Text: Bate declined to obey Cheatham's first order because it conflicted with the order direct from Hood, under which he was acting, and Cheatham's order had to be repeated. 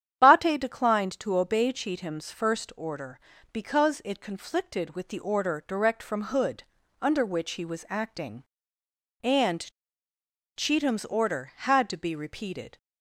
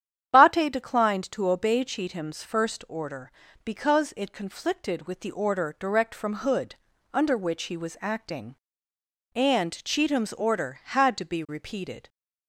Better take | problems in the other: second | starts louder than the rest; strong; until 1.2 s; 9.5 dB; strong in the second // pauses between "and" and "Cheatham's"; noticeable; at 9.7 s; 0.86 s long

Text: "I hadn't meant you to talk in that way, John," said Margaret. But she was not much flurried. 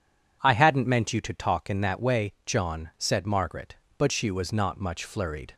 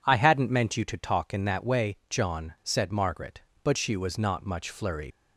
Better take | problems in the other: first | leaves "flurried" unfinished; at 5.1 s; 90 ms

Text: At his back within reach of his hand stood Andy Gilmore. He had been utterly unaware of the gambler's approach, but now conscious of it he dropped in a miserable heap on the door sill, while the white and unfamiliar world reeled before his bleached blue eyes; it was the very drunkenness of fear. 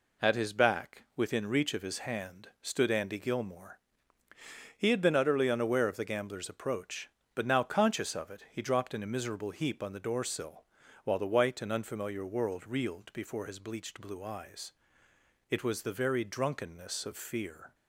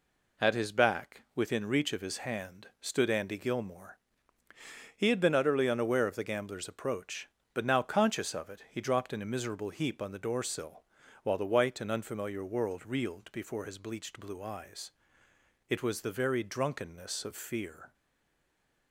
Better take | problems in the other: first | stays silent after the last word; from 17.9 s on; 1.0 s long

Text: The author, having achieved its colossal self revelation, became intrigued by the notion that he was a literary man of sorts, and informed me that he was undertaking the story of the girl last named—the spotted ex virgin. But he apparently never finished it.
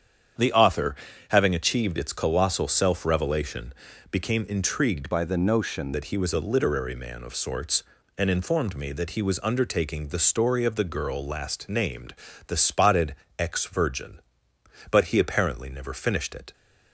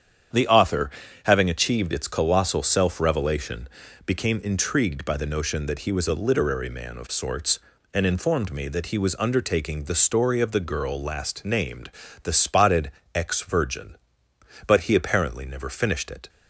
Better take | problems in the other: second | starts louder than the rest; strong; until 1.7 s; 8.5 dB; strong in the second // changes voice from "by" to "notion"; from 5.1 to 5.9 s; 0.8 s long // pauses between "spotted" and "ex"; slight; at 13.1 s; 0.24 s long; slight in the second

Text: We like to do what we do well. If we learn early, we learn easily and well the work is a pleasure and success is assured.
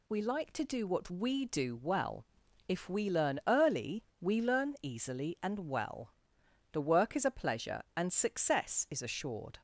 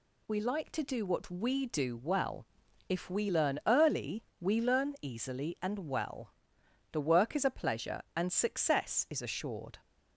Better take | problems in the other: neither | pauses between "well" and "the"; noticeable; the same in both

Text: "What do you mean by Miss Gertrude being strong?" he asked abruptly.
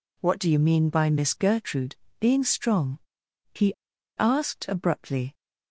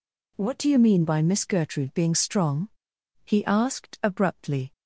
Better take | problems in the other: second | pauses between "Gertrude" and "being"; slight; at 1.9 s; 0.24 s long // pauses between "he" and "asked"; noticeable; at 3.7 s; 0.46 s long

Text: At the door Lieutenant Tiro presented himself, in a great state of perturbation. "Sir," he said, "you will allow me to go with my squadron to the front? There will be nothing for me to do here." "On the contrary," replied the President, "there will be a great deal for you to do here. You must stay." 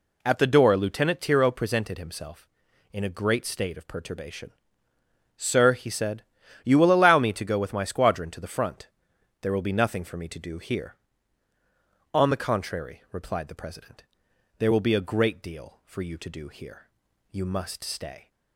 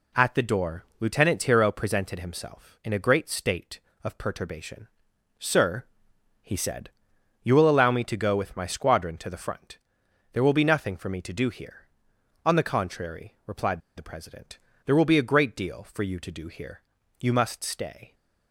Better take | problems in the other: first | pauses between "replied" and "the"; slight; at 13.8 s; 0.15 s long

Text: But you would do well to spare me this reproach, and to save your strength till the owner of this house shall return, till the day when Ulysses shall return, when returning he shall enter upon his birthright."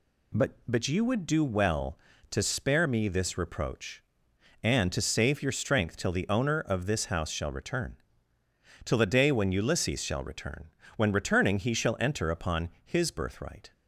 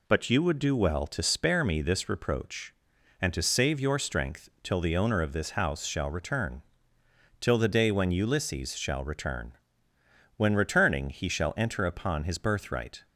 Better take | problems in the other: second | says "But" twice; at 0.6 s

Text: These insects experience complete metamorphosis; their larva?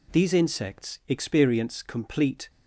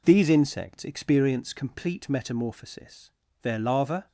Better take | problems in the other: second | stops before "metamorphosis their larva"; at 2.4 s

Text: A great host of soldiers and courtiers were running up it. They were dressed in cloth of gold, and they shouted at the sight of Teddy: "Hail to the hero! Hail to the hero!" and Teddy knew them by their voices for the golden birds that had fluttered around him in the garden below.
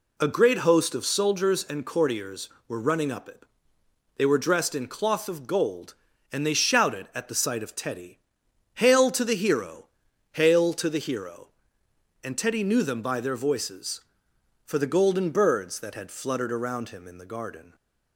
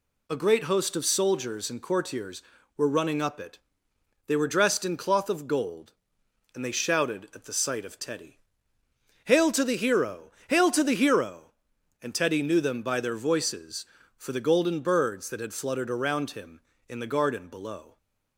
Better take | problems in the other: second | stops before "below"; at 17.7 s

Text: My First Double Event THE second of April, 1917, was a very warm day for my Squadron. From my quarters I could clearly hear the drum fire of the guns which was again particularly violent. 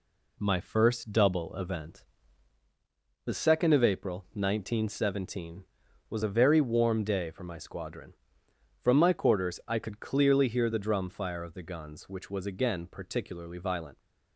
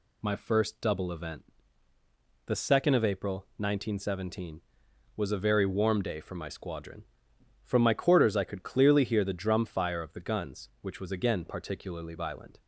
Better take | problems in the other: second | gets quieter; noticeable; throughout; 5 dB // pauses between "Event" and "THE"; at 2.0 s; 1.2 s long; also in the second

